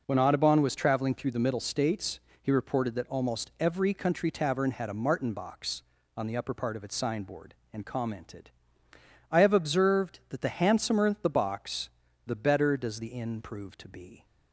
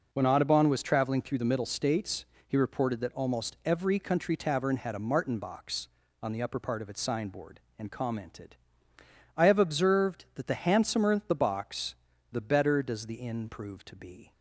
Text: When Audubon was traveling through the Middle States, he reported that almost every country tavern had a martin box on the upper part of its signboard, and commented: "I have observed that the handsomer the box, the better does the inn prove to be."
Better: neither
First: none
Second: none

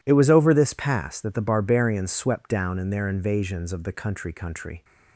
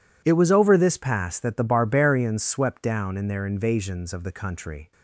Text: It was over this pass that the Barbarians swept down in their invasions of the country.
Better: second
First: says "country" twice; at 4.3 s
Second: none

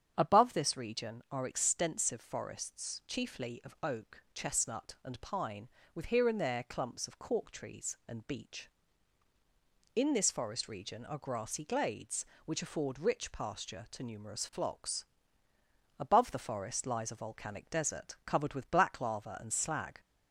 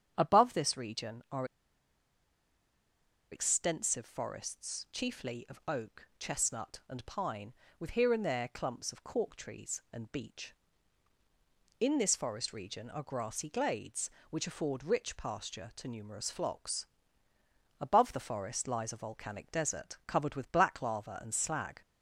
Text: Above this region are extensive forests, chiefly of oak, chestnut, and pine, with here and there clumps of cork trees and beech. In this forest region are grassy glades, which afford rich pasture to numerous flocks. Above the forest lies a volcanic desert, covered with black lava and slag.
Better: first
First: starts louder than the rest; strong; until 1.1 s; 8 dB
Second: starts louder than the rest; strong; until 1.1 s; 8 dB // pauses between "are" and "extensive"; strong; at 1.4 s; 1.8 s long

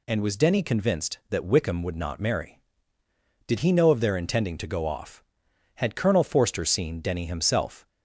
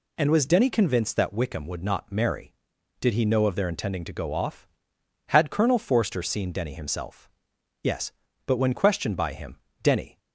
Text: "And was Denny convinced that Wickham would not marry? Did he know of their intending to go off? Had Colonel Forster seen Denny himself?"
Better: first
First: none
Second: goes on to say "Yes but when questioned by him Denny"; strong; from 7.8 s on; 2.3 s long

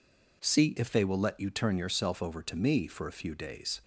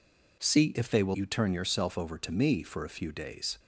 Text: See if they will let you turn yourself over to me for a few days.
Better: first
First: none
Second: skips "let"; at 1.1 s

